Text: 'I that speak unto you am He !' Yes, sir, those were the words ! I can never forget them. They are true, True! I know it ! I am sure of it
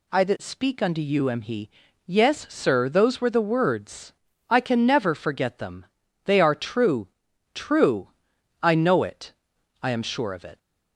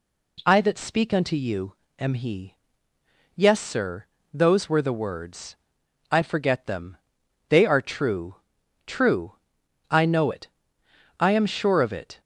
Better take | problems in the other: first | pauses between "you" and "am"; slight; at 1.7 s; 0.24 s long // skips "can never"; at 6.2 s

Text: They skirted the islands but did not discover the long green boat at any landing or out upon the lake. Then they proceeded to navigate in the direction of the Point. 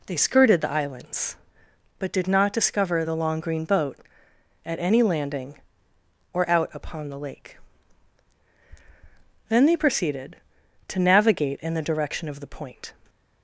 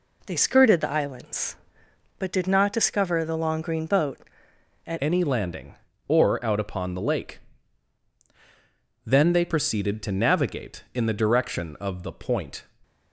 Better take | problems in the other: first | changes voice at "any"; from 5.0 s on; 7.6 s long

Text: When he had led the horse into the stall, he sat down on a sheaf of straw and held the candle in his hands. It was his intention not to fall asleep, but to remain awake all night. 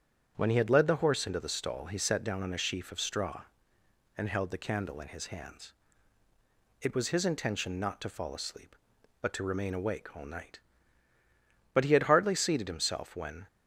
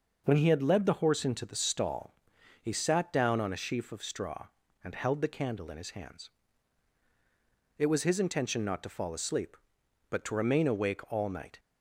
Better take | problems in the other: second | starts louder than the rest; strong; until 1.3 s; 7.5 dB // goes on to say "But he had hardly seated himself when"; strong; from 11.7 s on; 1.7 s long

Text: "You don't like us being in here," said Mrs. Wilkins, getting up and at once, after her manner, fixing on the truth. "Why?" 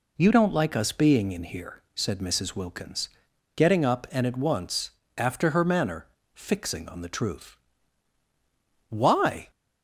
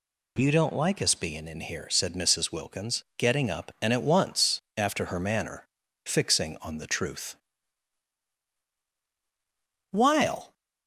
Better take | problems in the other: first | says "While" for "Why"; at 9.8 s

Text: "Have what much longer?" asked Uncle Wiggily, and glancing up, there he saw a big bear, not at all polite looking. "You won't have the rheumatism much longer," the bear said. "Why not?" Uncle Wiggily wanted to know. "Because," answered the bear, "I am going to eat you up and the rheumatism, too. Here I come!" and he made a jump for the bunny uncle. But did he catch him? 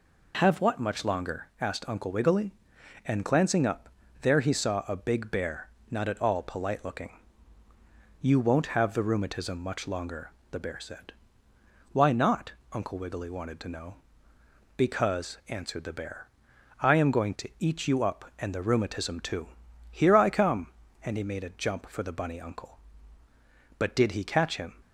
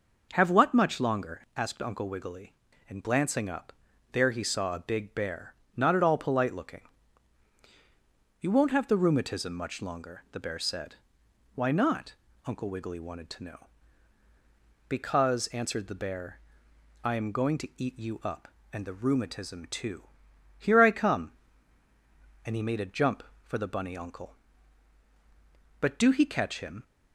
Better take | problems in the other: first | says "do" for "did"; at 25.9 s

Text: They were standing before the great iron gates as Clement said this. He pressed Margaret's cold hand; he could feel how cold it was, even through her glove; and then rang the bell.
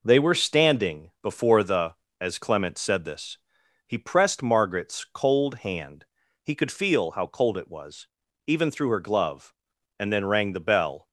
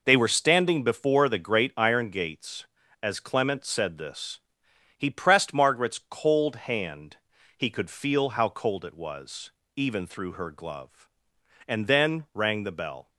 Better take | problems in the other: second | skips "great iron gates"; at 2.0 s

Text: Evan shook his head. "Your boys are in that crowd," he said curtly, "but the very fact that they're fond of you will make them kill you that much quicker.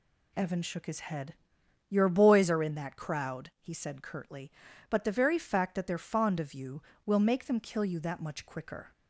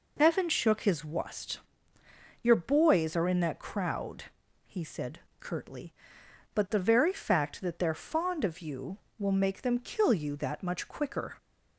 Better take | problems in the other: first | says "wust" for "head"; at 1.0 s // pauses between "said" and "curtly"; slight; at 5.1 s; 0.20 s long

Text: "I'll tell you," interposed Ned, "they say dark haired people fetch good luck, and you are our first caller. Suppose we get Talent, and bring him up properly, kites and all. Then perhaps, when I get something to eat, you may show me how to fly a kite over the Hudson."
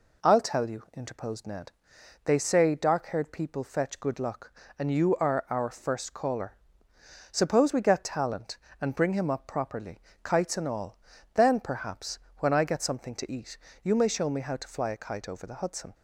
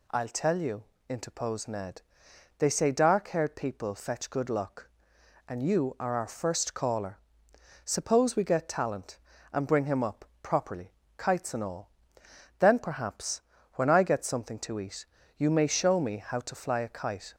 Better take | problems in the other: first | pauses between "up" and "properly"; slight; at 10.2 s; 0.18 s long // stops before "over the Hudson"; at 17.3 s

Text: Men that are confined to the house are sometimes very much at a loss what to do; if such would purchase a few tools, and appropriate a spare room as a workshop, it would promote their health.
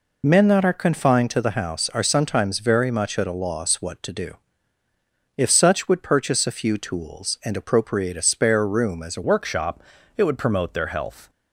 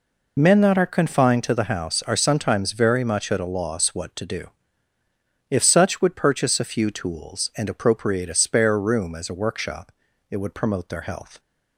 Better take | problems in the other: second | changes voice at "workshop"; from 9.2 s on; 2.0 s long

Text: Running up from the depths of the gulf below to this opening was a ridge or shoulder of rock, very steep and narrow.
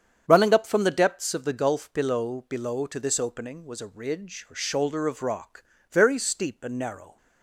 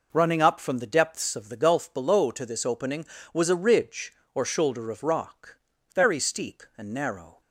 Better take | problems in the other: second | starts louder than the rest; strong; until 1.2 s; 8 dB // says "below" twice; at 2.4 s

